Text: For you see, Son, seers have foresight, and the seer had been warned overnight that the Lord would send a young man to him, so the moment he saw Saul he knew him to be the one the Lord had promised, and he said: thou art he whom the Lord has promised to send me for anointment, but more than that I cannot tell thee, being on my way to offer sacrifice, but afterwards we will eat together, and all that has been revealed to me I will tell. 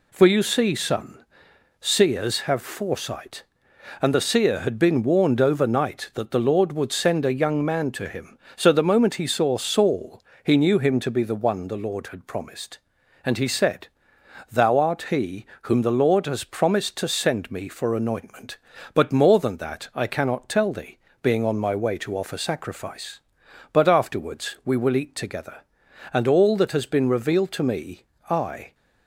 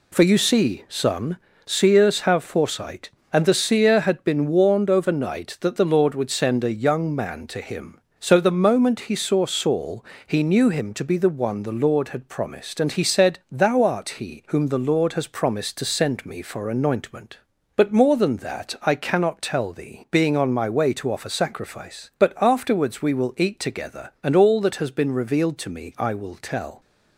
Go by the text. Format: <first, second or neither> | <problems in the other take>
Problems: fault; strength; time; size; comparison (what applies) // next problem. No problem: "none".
second | pauses between "Saul" and "he"; slight; at 10.2 s; 0.22 s long; slight in the second // pauses between "he" and "whom"; slight; at 15.4 s; 0.16 s long // pauses between "me" and "I"; slight; at 28.0 s; 0.26 s long // stops before "will tell"; at 28.7 s